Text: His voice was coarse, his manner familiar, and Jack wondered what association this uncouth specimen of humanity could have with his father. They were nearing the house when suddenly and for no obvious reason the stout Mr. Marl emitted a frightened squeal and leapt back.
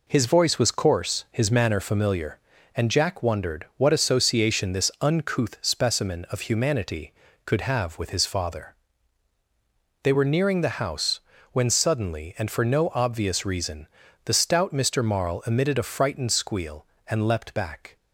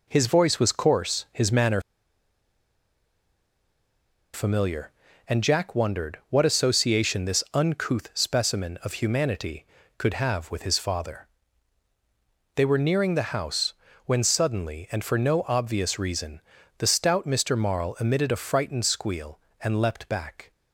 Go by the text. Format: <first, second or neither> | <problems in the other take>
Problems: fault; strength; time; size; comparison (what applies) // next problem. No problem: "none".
first | pauses between "manner" and "familiar"; strong; at 1.8 s; 2.5 s long // pauses between "house" and "when"; slight; at 13.7 s; 0.32 s long; slight in the first // pauses between "reason" and "the"; slight; at 16.4 s; 0.36 s long; slight in the first